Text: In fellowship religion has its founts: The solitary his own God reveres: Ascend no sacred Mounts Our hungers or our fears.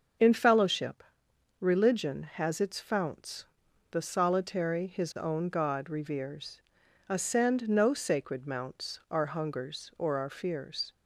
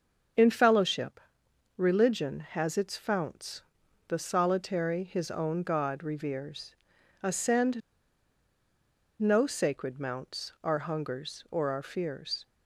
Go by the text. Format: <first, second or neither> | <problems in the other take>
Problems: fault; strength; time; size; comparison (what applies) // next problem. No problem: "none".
first | starts louder than the rest; until 1.9 s; 6.5 dB; also in the first // pauses between "fellowship" and "religion"; noticeable; at 1.2 s; 0.56 s long; noticeable in the first // pauses between "Ascend" and "no"; strong; at 7.8 s; 1.3 s long